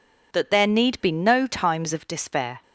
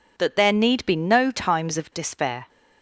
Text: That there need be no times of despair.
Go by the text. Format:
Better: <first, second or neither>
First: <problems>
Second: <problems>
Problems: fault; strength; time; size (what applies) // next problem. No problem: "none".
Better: neither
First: none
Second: none